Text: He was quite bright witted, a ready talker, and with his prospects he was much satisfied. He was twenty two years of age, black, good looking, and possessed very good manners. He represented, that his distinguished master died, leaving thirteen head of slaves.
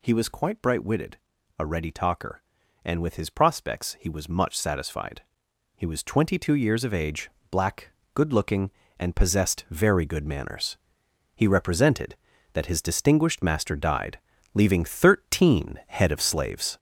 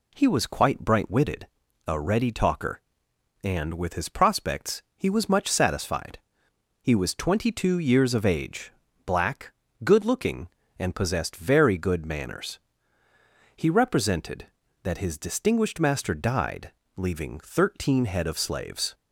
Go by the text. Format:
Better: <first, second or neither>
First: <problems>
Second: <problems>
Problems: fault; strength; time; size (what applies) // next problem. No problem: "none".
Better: second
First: gets louder; noticeable; throughout; 5.5 dB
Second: none